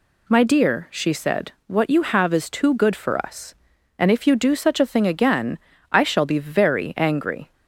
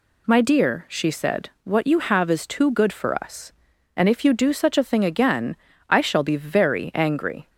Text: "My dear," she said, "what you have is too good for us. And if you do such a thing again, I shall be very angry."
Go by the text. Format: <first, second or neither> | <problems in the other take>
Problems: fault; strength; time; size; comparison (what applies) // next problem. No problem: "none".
neither | none